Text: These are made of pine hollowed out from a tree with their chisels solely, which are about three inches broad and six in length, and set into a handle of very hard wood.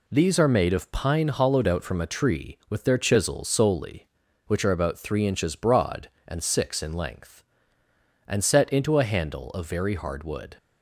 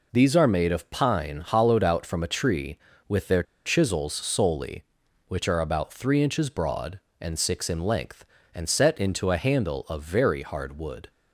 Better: first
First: none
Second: pauses between "their" and "chisels"; slight; at 3.4 s; 0.21 s long

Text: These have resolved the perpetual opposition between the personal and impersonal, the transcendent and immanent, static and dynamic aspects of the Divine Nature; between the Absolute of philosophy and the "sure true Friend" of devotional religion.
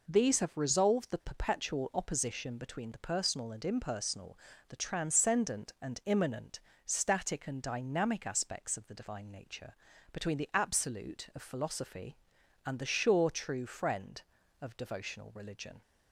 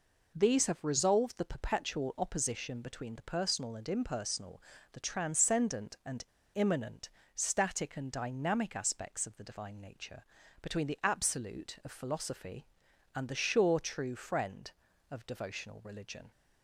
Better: first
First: none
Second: pauses between "and" and "immanent"; slight; at 6.2 s; 0.31 s long

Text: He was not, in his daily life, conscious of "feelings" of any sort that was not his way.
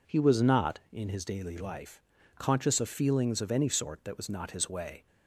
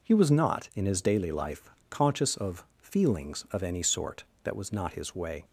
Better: neither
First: none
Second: none

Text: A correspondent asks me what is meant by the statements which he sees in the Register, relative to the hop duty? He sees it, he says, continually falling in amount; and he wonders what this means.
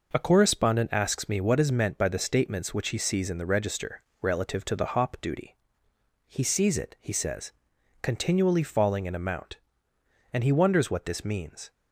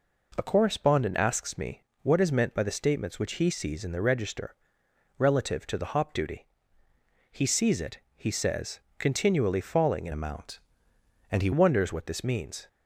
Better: first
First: none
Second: pauses between "me" and "what"; slight; at 1.8 s; 0.18 s long // changes voice from "amount" to "he"; from 10.1 to 11.4 s; 1.3 s long

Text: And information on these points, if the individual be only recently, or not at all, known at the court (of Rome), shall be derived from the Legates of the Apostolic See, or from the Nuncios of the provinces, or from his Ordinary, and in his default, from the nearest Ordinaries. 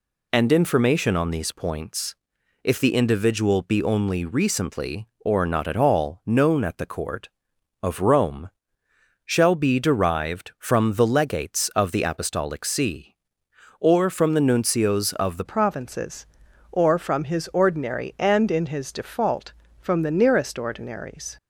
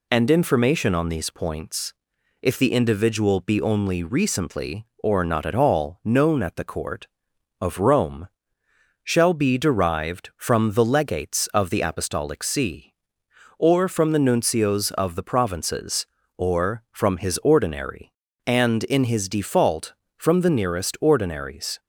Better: second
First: changes voice at "provinces"; from 15.4 s on; 5.9 s long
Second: none

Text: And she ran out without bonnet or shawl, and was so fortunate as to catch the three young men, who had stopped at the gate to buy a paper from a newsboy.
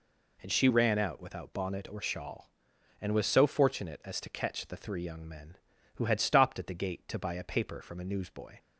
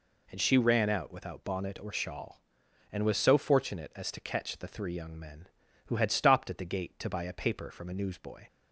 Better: neither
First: none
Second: none

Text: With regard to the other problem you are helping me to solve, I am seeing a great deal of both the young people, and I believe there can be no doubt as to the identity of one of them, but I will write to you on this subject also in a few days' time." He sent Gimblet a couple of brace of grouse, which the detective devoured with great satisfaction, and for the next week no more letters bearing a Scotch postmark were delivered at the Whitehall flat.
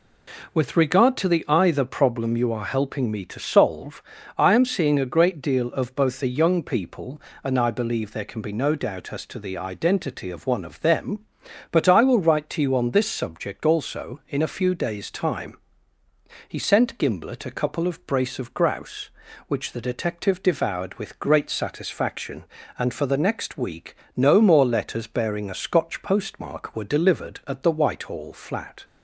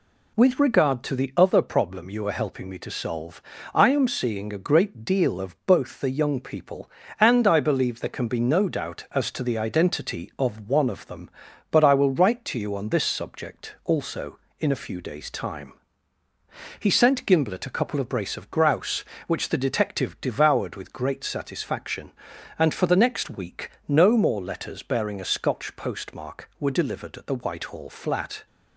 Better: second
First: says "either" for "other"; at 1.4 s // pauses between "week" and "no"; slight; at 23.9 s; 0.20 s long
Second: pauses between "week" and "no"; slight; at 23.6 s; 0.18 s long

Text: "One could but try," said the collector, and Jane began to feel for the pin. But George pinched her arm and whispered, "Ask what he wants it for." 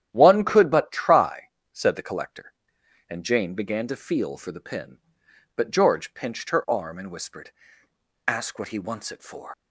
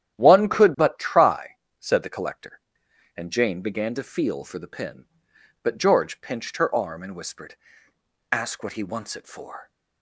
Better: second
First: starts louder than the rest; strong; until 1.1 s; 10.5 dB // leaves "for" unfinished; at 9.5 s; 110 ms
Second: starts louder than the rest; strong; until 1.2 s; 10.5 dB

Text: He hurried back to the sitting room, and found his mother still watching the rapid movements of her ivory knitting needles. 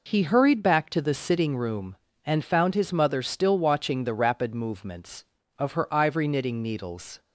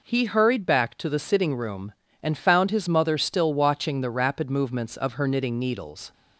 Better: first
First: none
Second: skips "ivory"; at 5.2 s

